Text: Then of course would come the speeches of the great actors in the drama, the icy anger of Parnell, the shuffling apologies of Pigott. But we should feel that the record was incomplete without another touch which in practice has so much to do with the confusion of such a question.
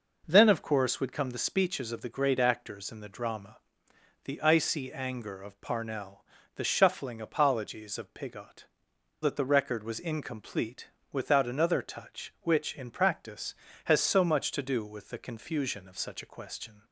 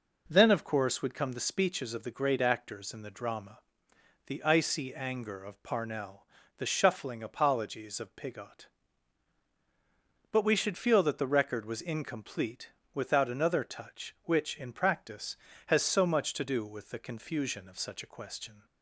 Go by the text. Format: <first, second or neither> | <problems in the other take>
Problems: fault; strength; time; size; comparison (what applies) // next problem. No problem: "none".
second | skips "But we should feel"; at 8.9 s // pauses between "incomplete" and "without"; slight; at 10.8 s; 0.22 s long; slight in the second